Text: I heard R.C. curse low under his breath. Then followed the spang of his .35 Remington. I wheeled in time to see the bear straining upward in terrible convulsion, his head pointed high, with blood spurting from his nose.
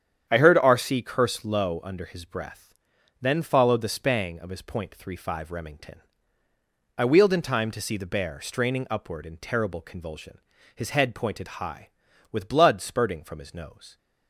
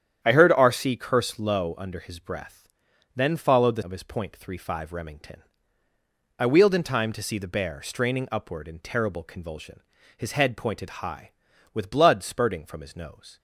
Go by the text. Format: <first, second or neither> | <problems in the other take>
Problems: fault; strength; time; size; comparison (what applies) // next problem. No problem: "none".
first | starts louder than the rest; strong; until 1.2 s; 9.5 dB; strong in the first // skips "spang"; at 3.8 s